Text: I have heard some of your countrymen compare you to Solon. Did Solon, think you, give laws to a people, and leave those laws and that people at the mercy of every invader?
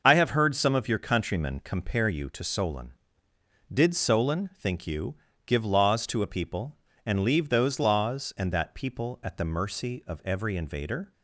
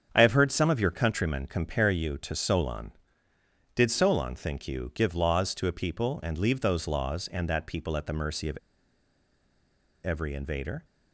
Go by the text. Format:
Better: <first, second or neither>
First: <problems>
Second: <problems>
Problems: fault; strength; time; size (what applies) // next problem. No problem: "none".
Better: first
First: starts louder than the rest; until 1.0 s; 6 dB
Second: starts louder than the rest; strong; until 1.1 s; 7.5 dB // pauses between "of" and "every"; strong; at 8.5 s; 1.4 s long